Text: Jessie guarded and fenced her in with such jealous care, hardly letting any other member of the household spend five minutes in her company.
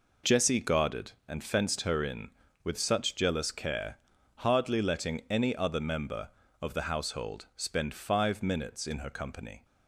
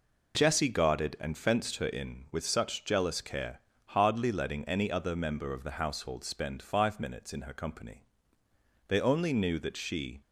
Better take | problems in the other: first | goes on to say "They only knew that she"; from 8.8 s on; 1.3 s long

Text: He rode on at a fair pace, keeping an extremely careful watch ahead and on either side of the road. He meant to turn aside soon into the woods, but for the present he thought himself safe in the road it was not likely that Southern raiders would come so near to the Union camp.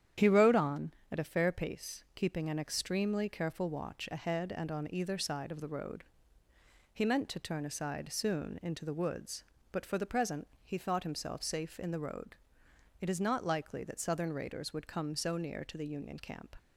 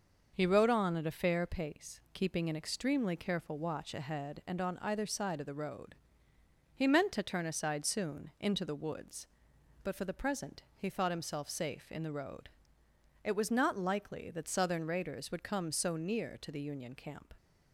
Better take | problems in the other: second | starts louder than the rest; strong; until 1.4 s; 9.5 dB; noticeable in the second // pauses between "present" and "he"; slight; at 10.4 s; 0.16 s long // pauses between "road" and "it"; noticeable; at 12.3 s; 0.66 s long; noticeable in the second // says "is" for "was"; at 13.0 s

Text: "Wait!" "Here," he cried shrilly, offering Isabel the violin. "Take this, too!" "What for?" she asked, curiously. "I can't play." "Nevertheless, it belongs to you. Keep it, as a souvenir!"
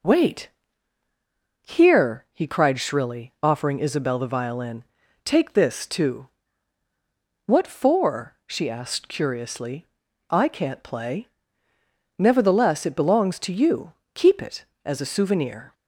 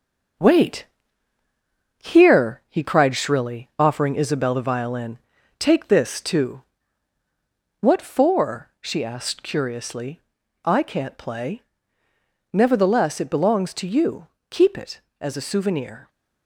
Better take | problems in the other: first | gets quieter; noticeable; throughout; 4 dB

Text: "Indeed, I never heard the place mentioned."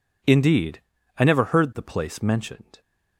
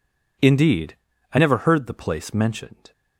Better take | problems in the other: neither | none

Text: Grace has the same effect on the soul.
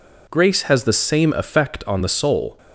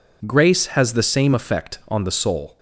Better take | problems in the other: neither | none

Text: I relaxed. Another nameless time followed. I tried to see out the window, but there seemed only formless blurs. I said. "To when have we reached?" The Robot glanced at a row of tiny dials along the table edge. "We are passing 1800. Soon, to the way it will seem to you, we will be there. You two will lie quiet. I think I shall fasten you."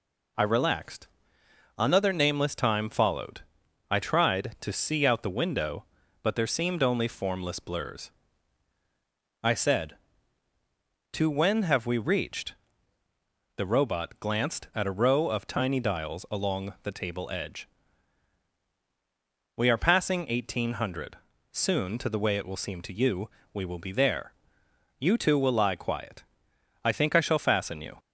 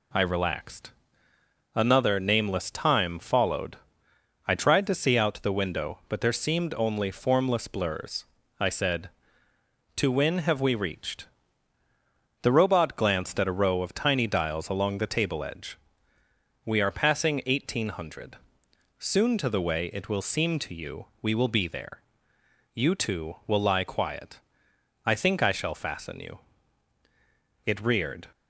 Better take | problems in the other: first | goes on to say "It reared"; noticeable; from 27.6 s on; 0.64 s long

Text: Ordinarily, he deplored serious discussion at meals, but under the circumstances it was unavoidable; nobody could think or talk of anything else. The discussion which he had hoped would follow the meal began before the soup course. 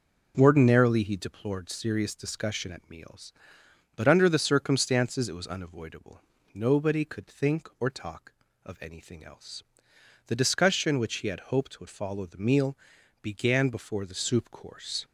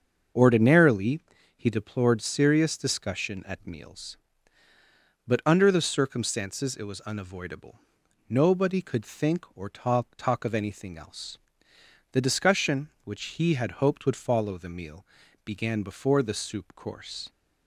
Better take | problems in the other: first | starts louder than the rest; until 1.7 s; 6.5 dB // says "talk" twice; at 10.1 s // pauses between "meal" and "began"; at 15.0 s; 0.40 s long; noticeable in the first

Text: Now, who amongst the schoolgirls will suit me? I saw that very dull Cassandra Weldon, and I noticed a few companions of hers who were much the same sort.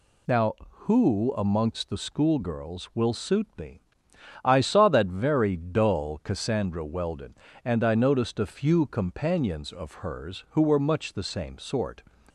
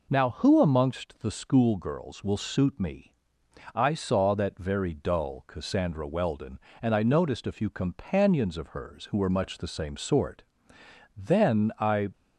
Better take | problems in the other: first | goes on to say "Then I"; noticeable; from 11.1 s on; 0.94 s long

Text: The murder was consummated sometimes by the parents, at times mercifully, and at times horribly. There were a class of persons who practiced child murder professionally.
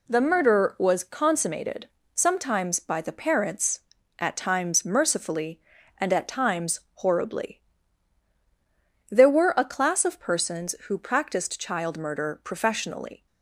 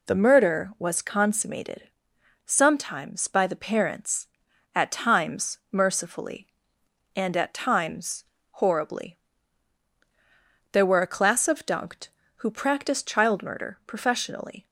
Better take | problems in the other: first | pauses between "consummated" and "sometimes"; noticeable; at 1.8 s; 0.62 s long; slight in the first // pauses between "times" and "horribly"; slight; at 8.2 s; 0.28 s long // says "dunked" for "persons"; at 11.6 s

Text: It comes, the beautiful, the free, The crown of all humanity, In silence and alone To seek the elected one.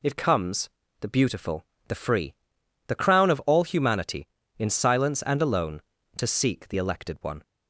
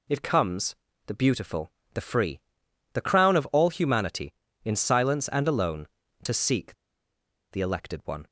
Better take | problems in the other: first | pauses between "seek" and "the"; noticeable; at 6.7 s; 0.77 s long

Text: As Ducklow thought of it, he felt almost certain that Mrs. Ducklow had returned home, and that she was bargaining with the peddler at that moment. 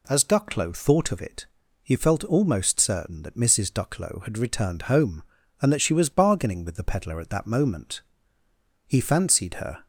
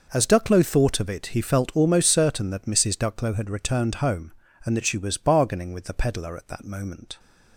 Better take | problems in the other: second | goes on to say "He fancied her"; noticeable; from 8.8 s on; 1.0 s long

